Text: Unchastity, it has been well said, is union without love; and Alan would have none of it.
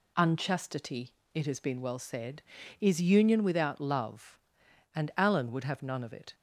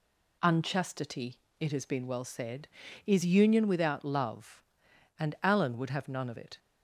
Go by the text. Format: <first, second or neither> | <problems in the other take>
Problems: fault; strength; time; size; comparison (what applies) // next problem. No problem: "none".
neither | none